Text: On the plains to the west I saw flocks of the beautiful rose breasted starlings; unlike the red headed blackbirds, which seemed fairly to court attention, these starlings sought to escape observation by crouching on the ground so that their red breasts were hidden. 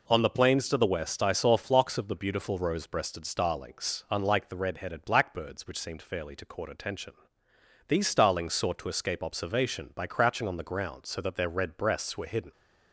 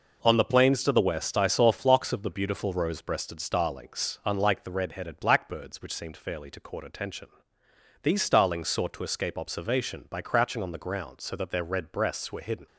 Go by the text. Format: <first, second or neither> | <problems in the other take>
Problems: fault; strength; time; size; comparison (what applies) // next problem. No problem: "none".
first | gets quieter; throughout; 7 dB